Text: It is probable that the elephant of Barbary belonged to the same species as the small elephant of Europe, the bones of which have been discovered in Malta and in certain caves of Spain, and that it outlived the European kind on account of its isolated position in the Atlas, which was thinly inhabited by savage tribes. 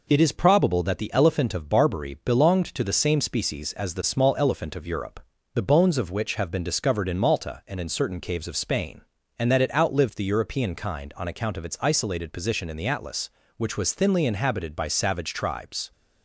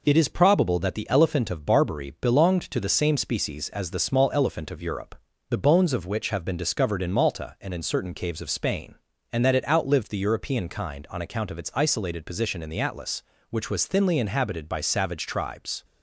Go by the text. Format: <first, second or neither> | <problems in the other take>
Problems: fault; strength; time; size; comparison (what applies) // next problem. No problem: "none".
neither | none